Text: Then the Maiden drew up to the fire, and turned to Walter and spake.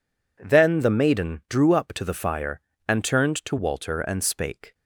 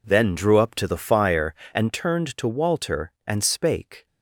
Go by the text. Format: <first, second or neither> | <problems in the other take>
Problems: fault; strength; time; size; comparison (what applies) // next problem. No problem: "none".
first | skips "the Maiden"; at 0.3 s